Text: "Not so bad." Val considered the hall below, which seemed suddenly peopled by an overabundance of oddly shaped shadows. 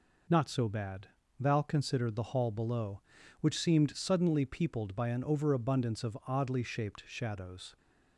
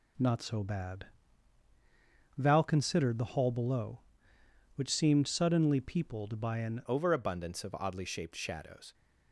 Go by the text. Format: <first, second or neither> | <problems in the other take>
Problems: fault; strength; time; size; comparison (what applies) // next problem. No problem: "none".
first | changes voice at "overabundance"; from 6.8 s on; 2.1 s long